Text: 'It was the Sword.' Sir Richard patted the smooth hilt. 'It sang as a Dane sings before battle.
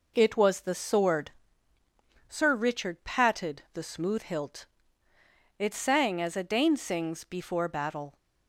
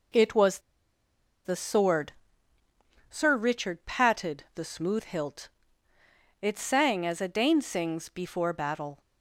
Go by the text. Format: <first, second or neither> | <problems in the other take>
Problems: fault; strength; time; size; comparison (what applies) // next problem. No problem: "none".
first | pauses between "was" and "the"; noticeable; at 0.5 s; 0.86 s long